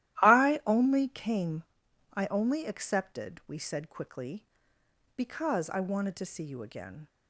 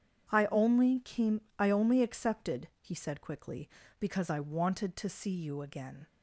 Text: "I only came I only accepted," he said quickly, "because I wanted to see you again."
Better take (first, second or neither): second